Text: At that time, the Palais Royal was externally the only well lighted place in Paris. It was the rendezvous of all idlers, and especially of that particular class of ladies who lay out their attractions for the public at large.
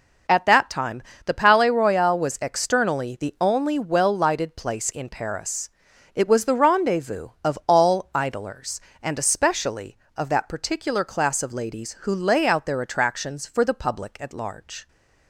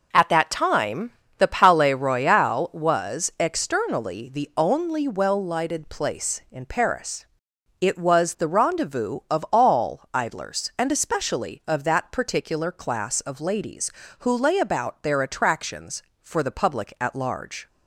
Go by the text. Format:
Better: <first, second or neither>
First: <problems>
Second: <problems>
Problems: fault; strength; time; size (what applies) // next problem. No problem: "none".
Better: first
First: none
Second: says "about" for "out"; at 14.5 s